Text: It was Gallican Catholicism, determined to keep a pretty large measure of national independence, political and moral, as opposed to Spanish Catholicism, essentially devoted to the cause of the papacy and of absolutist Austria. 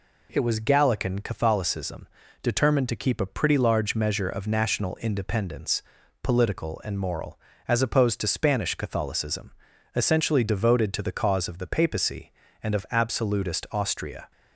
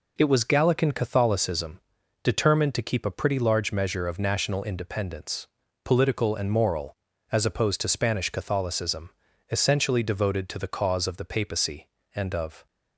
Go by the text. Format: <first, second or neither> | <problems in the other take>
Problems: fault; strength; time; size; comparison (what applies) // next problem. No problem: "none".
first | stops before "absolutist Austria"; at 12.6 s